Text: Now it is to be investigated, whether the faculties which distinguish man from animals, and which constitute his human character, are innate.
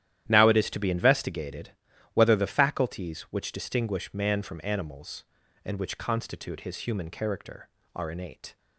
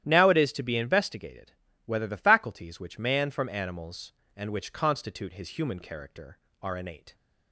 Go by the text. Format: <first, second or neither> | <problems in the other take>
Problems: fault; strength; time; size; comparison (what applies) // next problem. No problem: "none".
first | starts louder than the rest; strong; until 1.0 s; 12 dB; strong in the first // skips "distinguish"; at 2.9 s